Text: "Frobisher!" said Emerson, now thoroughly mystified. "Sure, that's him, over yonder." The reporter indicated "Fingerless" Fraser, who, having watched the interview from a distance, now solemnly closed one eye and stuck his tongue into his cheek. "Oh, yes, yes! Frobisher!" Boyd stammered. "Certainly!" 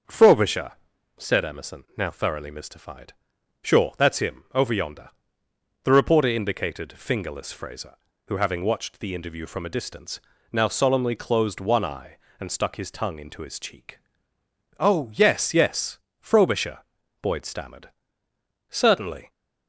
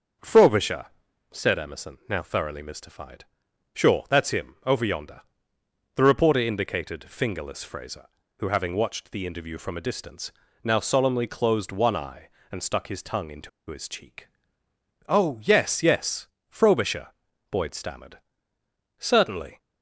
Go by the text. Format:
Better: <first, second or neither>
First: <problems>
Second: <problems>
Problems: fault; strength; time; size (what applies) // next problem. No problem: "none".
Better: first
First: starts louder than the rest; until 1.5 s; 6.5 dB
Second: starts louder than the rest; until 1.6 s; 7 dB // pauses between "into" and "his"; slight; at 13.4 s; 0.20 s long